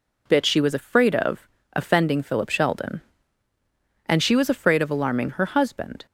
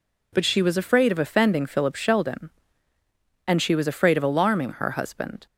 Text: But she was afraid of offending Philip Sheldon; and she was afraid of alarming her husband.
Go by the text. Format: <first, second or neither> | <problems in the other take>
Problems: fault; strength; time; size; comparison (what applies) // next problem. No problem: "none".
second | says "Bit" for "But"; at 0.2 s // pauses between "of" and "offending"; slight; at 1.4 s; 0.26 s long